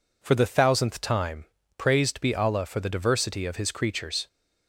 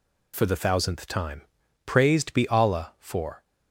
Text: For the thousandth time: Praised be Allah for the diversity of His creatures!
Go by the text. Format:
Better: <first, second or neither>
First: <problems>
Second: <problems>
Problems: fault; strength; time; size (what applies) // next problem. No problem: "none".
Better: first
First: none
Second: stops before "the diversity of His creatures"; at 3.4 s